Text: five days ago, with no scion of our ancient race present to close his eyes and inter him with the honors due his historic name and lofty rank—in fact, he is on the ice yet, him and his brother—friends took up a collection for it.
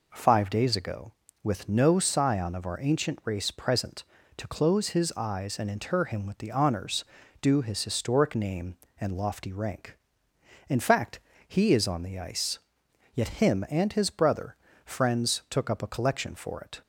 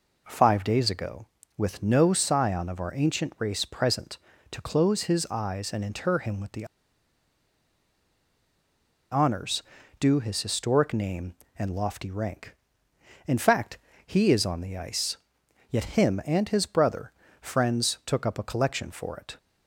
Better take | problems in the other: first | pauses between "the" and "honors"; strong; at 6.6 s; 2.4 s long // pauses between "honors" and "due"; at 9.6 s; 0.38 s long; also in the first // pauses between "ice" and "yet"; noticeable; at 15.1 s; 0.52 s long; noticeable in the first

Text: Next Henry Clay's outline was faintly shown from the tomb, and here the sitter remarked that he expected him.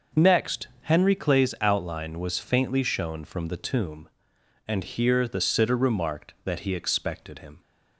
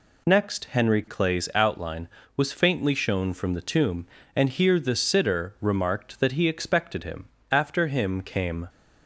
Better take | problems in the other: first | goes on to say "After him came"; noticeable; from 7.5 s on; 1.1 s long

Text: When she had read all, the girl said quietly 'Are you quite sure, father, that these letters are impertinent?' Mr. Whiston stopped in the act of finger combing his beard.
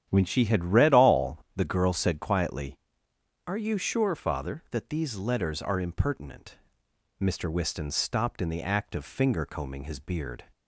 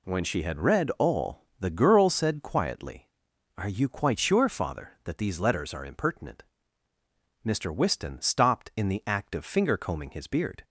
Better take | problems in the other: second | starts louder than the rest; strong; until 1.1 s; 10 dB // skips "quite"; at 3.7 s

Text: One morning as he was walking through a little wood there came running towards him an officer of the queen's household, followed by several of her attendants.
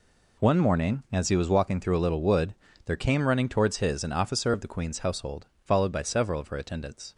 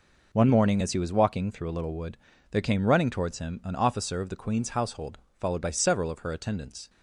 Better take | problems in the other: second | pauses between "wood" and "there"; slight; at 2.5 s; 0.30 s long; slight in the second // says "his" for "him"; at 3.7 s

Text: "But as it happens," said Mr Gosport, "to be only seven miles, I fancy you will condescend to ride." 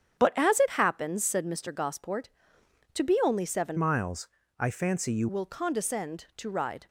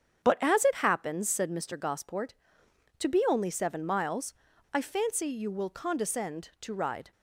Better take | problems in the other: second | starts louder than the rest; strong; until 1.2 s; 8.5 dB; strong in the second // changes voice from "miles" to "you"; from 3.7 to 5.2 s; 1.5 s long

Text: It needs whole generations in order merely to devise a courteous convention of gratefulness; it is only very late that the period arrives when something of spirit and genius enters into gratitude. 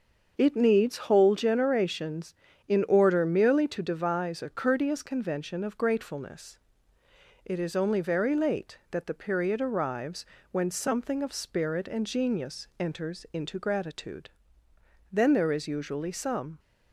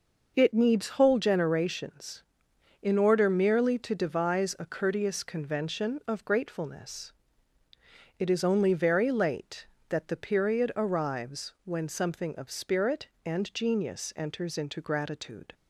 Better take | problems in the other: second | starts louder than the rest; until 1.3 s; 6.5 dB // pauses between "arrives" and "when"; slight; at 10.2 s; 0.24 s long // goes on to say "Then there is usually some"; from 15.1 s on; 1.4 s long

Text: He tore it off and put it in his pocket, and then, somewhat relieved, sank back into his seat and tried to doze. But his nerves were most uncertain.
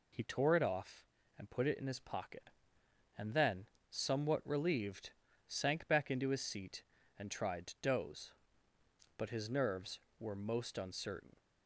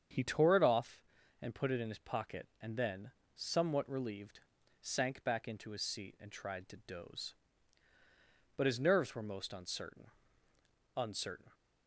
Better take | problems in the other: first | starts louder than the rest; strong; until 1.5 s; 7.5 dB // says "uncertain" twice; at 10.9 s

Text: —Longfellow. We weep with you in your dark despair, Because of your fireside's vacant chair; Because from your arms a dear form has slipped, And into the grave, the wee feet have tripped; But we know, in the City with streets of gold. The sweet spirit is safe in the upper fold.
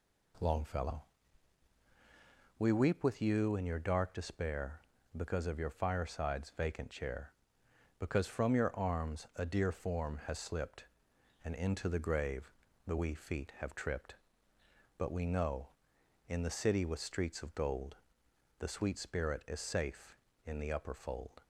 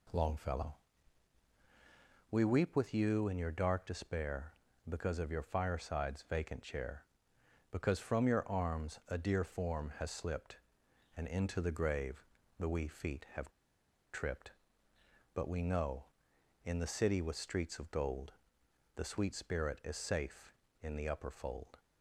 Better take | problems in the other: first | pauses between "have" and "tripped"; noticeable; at 13.4 s; 0.63 s long

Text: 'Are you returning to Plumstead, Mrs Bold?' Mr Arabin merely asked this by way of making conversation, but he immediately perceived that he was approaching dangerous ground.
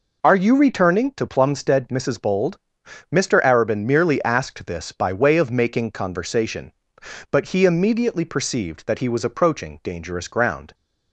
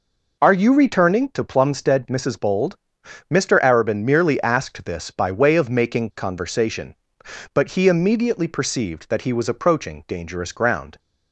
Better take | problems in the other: neither | none

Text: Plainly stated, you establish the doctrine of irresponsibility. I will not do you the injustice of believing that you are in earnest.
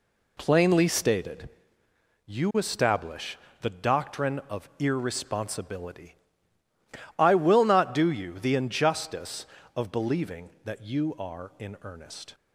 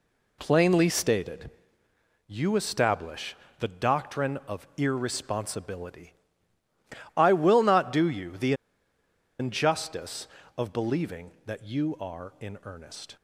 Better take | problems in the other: first | pauses between "establish" and "the"; slight; at 3.3 s; 0.24 s long; slight in the first // pauses between "the" and "injustice"; noticeable; at 8.5 s; 0.86 s long

